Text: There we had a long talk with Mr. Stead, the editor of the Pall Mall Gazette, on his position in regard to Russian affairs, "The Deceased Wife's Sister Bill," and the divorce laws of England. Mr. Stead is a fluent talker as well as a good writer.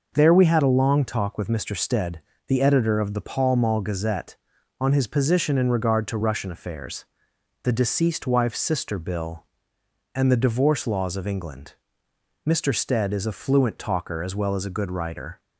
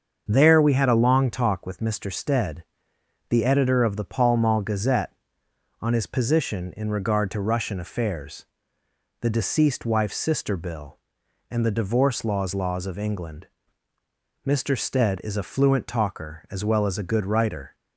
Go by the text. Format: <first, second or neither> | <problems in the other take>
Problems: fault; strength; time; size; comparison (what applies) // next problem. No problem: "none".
first | starts louder than the rest; until 1.3 s; 7 dB // says "laws" twice; at 12.5 s